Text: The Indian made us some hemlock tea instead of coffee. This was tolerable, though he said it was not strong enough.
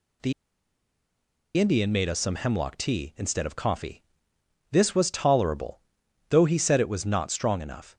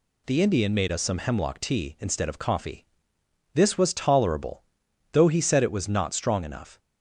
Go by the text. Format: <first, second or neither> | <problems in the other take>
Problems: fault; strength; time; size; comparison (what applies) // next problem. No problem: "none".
second | pauses between "The" and "Indian"; strong; at 0.3 s; 1.2 s long